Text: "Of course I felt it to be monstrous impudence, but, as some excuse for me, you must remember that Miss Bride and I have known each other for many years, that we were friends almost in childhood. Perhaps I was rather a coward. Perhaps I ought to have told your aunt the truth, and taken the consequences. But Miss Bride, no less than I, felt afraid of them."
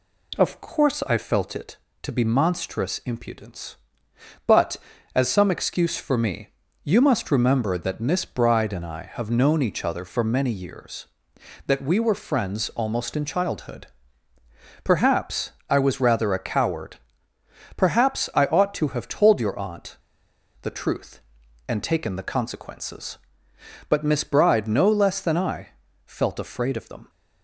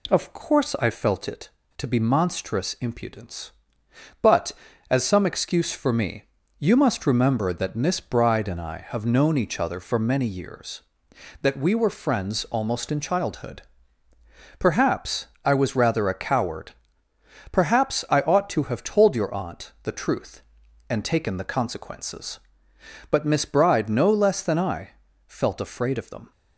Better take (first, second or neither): second